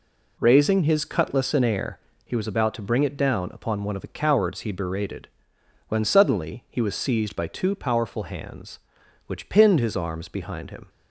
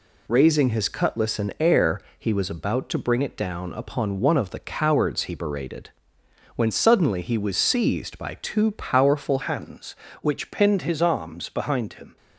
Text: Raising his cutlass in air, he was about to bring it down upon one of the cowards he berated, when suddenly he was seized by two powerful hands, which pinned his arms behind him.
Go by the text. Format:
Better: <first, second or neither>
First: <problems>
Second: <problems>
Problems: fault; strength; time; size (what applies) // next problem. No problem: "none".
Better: first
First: none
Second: changes voice at "hands"; from 9.4 s on; 2.7 s long